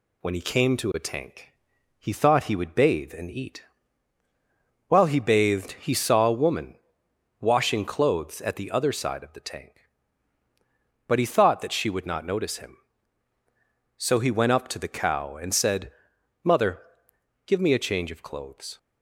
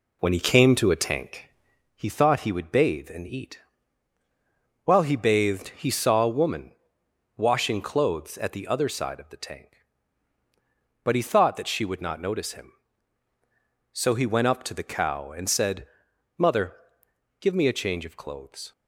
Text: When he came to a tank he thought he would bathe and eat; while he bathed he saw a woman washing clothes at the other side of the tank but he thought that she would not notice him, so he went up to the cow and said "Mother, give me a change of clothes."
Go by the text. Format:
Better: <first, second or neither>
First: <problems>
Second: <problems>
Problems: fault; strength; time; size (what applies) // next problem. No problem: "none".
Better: first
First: pauses between "tank" and "he"; noticeable; at 1.4 s; 0.50 s long // pauses between "woman" and "washing"; noticeable; at 6.7 s; 0.66 s long // pauses between "said" and "Mother"; noticeable; at 15.9 s; 0.50 s long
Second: starts louder than the rest; slight; until 1.9 s; 2.5 dB // pauses between "tank" and "he"; noticeable; at 1.4 s; 0.50 s long // pauses between "woman" and "washing"; noticeable; at 6.7 s; 0.66 s long // pauses between "said" and "Mother"; noticeable; at 15.8 s; 0.48 s long